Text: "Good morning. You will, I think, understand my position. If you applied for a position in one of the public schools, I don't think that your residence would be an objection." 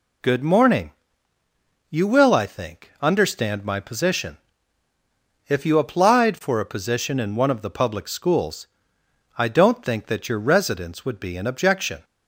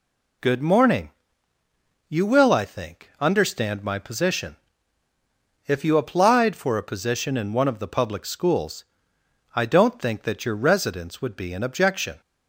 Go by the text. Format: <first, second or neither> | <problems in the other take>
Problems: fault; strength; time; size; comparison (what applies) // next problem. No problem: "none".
neither | none